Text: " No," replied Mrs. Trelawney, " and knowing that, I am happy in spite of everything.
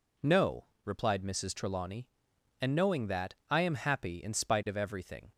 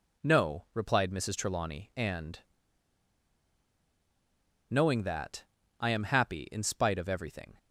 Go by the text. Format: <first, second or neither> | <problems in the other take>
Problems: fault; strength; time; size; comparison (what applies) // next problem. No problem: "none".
first | pauses between "and" and "knowing"; strong; at 2.3 s; 2.3 s long